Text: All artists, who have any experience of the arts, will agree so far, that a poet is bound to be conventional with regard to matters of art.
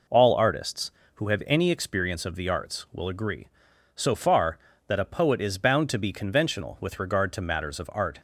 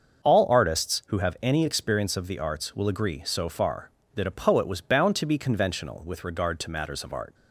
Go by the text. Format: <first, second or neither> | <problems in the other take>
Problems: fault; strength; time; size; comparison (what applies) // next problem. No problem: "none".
first | starts louder than the rest; until 1.3 s; 6.5 dB // says "was" for "is"; at 4.6 s